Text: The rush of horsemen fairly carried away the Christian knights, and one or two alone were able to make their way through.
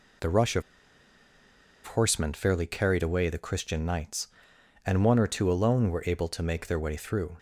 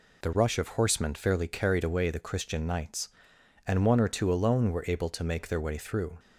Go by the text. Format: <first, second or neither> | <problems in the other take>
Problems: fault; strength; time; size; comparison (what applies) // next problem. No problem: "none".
second | pauses between "of" and "horsemen"; at 0.6 s; 1.2 s long